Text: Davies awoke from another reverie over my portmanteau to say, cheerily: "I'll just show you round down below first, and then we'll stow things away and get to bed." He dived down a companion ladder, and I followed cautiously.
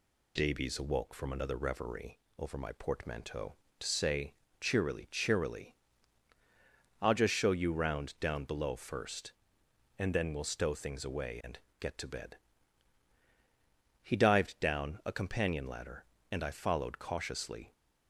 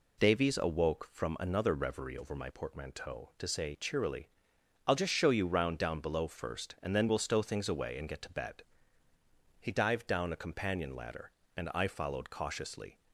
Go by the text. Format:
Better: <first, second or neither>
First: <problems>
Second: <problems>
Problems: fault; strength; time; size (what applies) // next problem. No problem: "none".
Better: second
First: pauses between "reverie" and "over"; slight; at 2.1 s; 0.20 s long // says "cheerily" twice; at 5.1 s // pauses between "and" and "get"; slight; at 11.5 s; 0.22 s long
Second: none